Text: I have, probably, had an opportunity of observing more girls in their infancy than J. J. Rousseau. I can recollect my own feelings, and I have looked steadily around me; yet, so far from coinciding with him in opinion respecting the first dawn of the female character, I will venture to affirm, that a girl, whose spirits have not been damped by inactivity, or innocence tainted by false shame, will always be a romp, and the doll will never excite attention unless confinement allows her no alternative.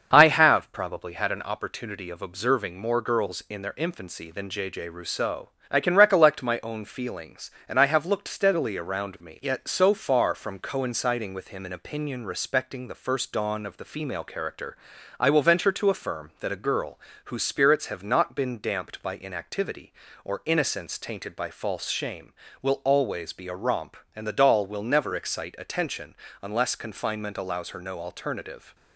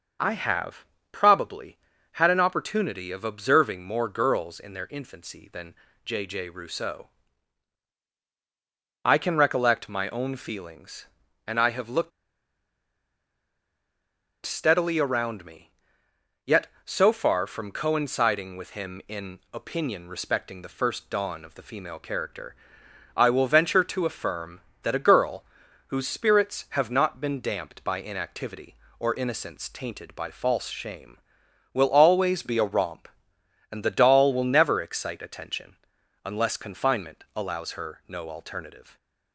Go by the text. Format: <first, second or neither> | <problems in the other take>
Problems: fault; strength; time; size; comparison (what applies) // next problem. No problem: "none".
first | starts louder than the rest; until 1.4 s; 6.5 dB; also in the first // pauses between "than" and "J"; slight; at 5.7 s; 0.32 s long // pauses between "looked" and "steadily"; strong; at 12.1 s; 2.3 s long // pauses between "attention" and "unless"; noticeable; at 35.7 s; 0.48 s long; slight in the first